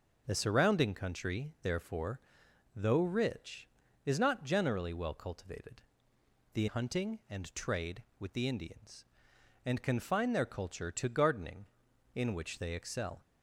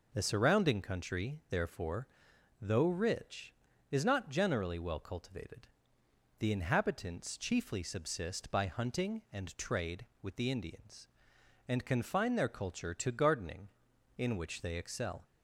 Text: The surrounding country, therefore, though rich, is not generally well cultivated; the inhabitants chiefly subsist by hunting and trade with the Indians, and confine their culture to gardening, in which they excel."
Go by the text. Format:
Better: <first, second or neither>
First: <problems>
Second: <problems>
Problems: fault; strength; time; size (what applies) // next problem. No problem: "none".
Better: second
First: skips "inhabitants chiefly subsist by"; at 6.6 s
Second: none